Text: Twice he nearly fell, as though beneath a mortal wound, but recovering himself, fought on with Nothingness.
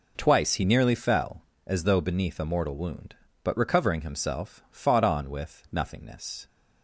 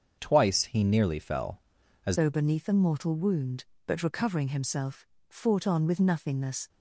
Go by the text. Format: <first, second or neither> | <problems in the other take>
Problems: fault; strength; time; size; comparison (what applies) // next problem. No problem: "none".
first | starts louder than the rest; until 1.2 s; 6.5 dB // changes voice at "though"; from 2.1 s on; 4.5 s long